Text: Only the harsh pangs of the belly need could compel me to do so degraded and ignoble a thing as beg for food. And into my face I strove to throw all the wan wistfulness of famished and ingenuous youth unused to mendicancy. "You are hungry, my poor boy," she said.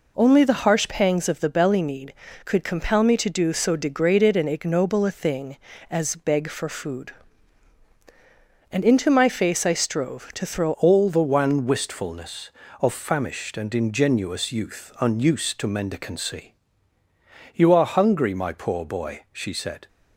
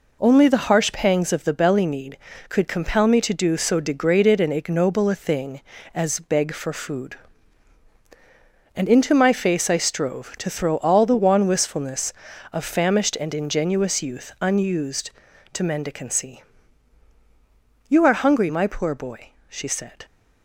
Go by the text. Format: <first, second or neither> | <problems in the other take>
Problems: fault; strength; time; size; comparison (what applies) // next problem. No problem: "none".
second | changes voice at "all"; from 10.7 s on; 9.1 s long